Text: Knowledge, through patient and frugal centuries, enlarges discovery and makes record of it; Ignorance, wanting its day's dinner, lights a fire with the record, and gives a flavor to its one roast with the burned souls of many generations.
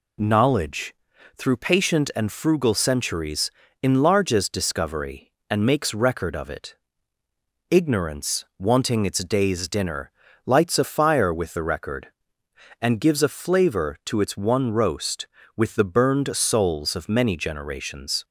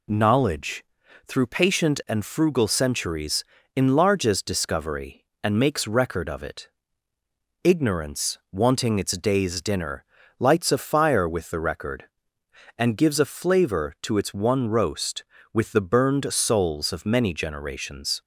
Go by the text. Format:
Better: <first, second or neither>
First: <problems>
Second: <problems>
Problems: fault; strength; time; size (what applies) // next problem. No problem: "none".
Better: neither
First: none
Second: none